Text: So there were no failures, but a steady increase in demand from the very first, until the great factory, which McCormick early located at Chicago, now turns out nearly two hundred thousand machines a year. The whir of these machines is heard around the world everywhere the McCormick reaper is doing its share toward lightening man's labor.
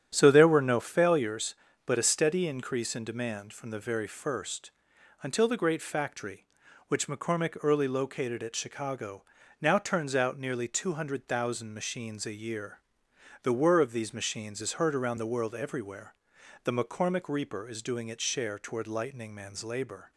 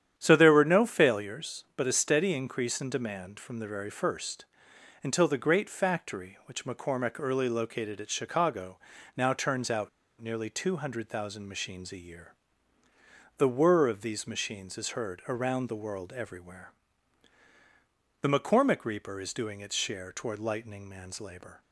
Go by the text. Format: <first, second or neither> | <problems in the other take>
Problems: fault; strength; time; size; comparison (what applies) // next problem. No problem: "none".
first | starts louder than the rest; strong; until 1.1 s; 9.5 dB; strong in the first // pauses between "out" and "nearly"; slight; at 9.8 s; 0.31 s long // pauses between "everywhere" and "the"; strong; at 16.7 s; 1.5 s long; noticeable in the first